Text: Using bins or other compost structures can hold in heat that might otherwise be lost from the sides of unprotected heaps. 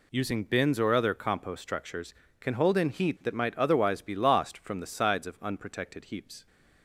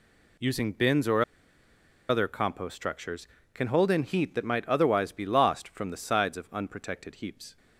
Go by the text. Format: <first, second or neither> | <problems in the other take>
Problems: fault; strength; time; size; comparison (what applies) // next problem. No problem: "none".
first | pauses between "or" and "other"; noticeable; at 1.2 s; 0.85 s long